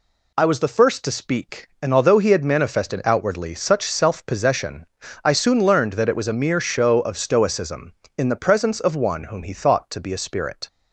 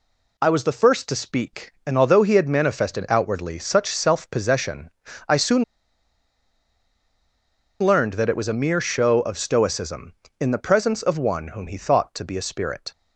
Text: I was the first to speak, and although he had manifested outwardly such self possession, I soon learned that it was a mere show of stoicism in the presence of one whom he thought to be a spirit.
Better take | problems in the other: first | pauses between "soon" and "learned"; strong; at 5.6 s; 2.1 s long

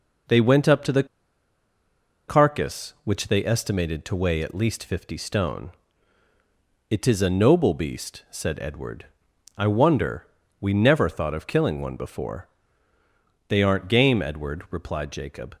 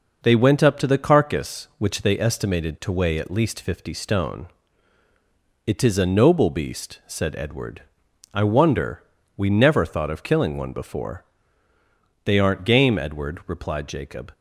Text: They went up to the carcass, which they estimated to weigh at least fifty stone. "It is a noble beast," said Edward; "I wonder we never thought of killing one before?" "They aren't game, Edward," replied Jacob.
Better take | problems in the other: second | pauses between "the" and "carcass"; at 1.0 s; 1.2 s long // pauses between "wonder" and "we"; slight; at 10.2 s; 0.32 s long; slight in the second

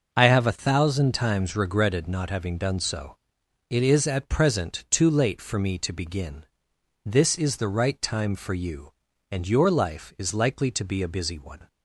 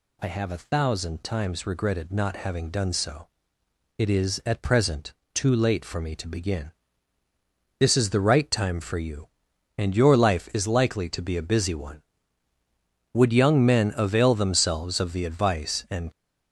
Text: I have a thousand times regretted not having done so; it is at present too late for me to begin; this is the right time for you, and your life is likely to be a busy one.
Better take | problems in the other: first | pauses between "present" and "too"; slight; at 5.1 s; 0.20 s long // goes on to say "Would young men avail themselves of the advice and"; strong; from 13.1 s on; 2.9 s long

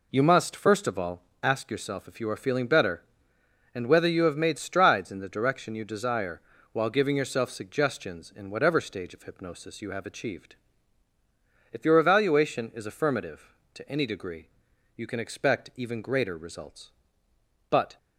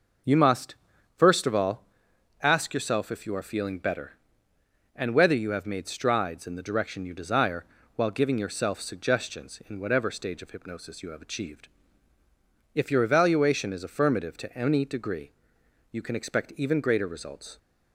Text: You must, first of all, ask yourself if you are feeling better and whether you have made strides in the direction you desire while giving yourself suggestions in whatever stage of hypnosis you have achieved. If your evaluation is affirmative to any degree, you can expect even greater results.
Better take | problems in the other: second | pauses between "desire" and "while"; slight; at 6.4 s; 0.32 s long; slight in the second // goes on to say "But"; slight; from 17.6 s on; 0.28 s long

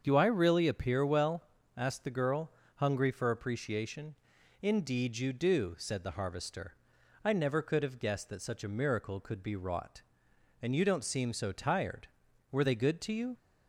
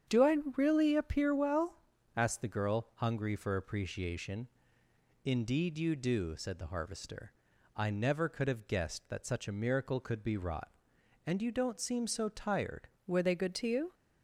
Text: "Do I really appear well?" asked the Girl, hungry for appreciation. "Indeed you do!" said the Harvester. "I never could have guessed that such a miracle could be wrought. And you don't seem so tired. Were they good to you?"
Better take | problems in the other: first | starts louder than the rest; strong; until 1.2 s; 8 dB; also in the first // pauses between "I" and "really"; slight; at 0.3 s; 0.18 s long // changes voice at "Were"; from 13.0 s on; 0.9 s long

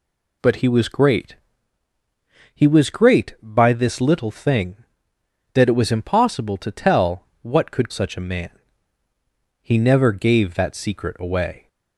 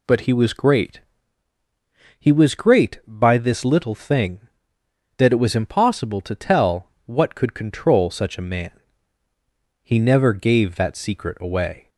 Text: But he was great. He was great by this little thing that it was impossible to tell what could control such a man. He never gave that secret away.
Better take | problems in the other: second | pauses between "tell" and "what"; slight; at 7.2 s; 0.18 s long; slight in the second // skips "control"; at 7.9 s

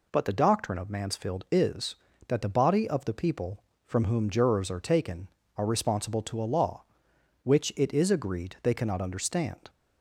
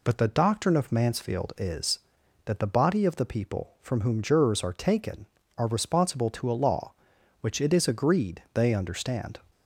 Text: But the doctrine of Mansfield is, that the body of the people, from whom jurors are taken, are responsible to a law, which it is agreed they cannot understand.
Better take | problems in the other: first | skips "cannot"; at 8.7 s

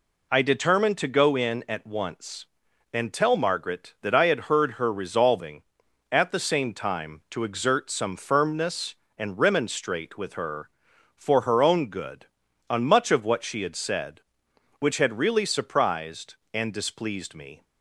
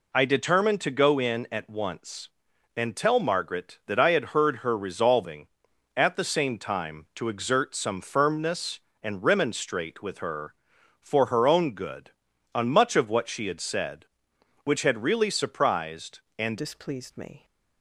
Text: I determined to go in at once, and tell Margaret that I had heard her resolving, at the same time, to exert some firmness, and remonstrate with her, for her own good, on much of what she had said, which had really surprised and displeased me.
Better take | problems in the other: first | changes voice at "displeased"; from 16.5 s on; 0.9 s long

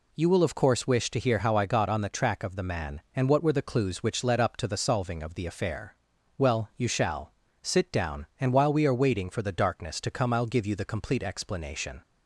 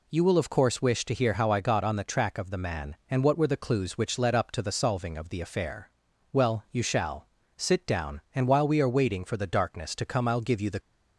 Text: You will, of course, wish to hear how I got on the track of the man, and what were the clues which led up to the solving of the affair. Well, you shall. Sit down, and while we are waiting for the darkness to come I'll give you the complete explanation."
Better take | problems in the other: first | stops before "complete explanation"; at 10.8 s

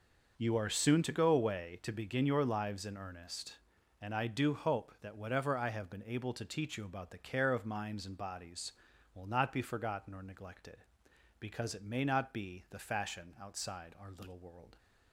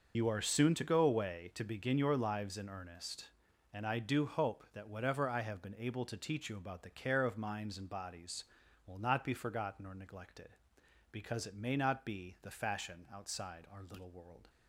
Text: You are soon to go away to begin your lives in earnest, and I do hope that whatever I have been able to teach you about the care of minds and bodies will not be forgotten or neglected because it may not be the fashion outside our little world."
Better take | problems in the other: first | loses the start of "You"; at 0.1 s; 60 ms

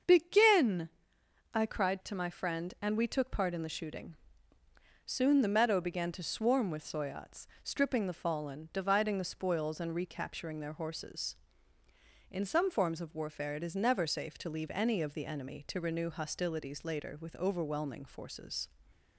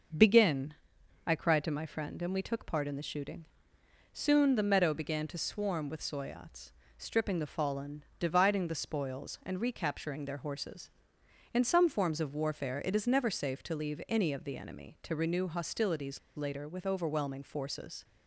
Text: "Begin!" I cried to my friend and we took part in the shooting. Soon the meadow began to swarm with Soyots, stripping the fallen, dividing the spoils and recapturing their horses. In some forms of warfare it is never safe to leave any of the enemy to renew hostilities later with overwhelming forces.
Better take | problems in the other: first | starts louder than the rest; noticeable; until 1.6 s; 6 dB; also in the first // pauses between "hostilities" and "later"; slight; at 16.1 s; 0.16 s long

